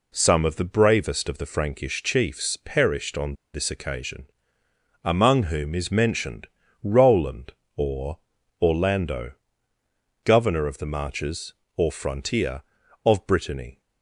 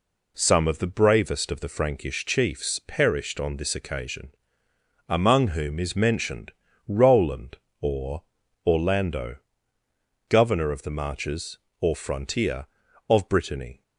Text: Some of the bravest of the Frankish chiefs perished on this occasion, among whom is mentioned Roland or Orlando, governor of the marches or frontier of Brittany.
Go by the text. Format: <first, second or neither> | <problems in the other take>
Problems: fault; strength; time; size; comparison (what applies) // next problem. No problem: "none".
second | pauses between "on" and "this"; slight; at 3.3 s; 0.19 s long // pauses between "mentioned" and "Roland"; at 6.4 s; 0.38 s long; also in the second // pauses between "or" and "Orlando"; at 8.1 s; 0.42 s long; also in the second